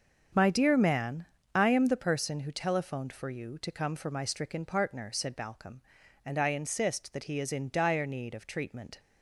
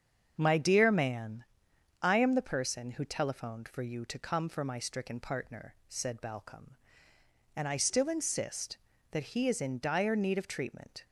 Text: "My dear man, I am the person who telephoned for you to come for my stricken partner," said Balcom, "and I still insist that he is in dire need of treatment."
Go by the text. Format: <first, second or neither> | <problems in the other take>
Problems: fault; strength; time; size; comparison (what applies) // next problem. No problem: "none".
second | starts louder than the rest; until 1.6 s; 6.5 dB; strong in the second // skips "still"; at 6.4 s